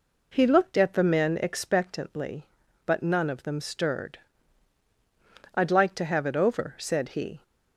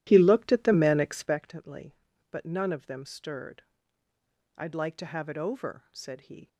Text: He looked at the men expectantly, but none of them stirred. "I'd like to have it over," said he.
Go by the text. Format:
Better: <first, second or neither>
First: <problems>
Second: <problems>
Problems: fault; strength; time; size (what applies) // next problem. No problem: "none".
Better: first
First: none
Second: starts louder than the rest; strong; until 1.5 s; 13.5 dB